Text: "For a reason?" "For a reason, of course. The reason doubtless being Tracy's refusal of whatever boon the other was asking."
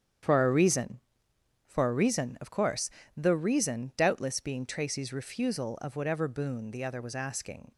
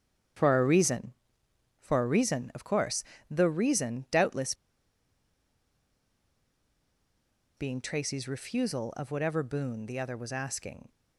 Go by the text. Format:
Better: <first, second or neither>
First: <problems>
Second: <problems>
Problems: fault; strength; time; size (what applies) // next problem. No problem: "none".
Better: first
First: starts louder than the rest; strong; until 1.8 s; 8.5 dB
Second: starts louder than the rest; strong; until 2.0 s; 8.5 dB // pauses between "doubtless" and "being"; strong; at 4.5 s; 3.0 s long